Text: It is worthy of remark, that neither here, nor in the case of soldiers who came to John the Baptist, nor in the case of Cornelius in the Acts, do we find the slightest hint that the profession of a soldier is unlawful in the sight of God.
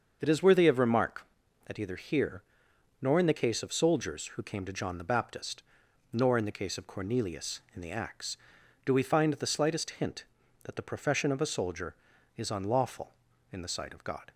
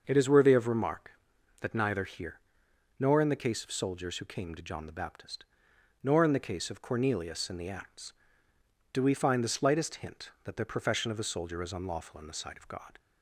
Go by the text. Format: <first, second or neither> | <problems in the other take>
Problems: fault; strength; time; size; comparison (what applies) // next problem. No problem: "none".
second | starts louder than the rest; until 1.2 s; 6.5 dB; also in the second // says "either" for "neither"; at 1.7 s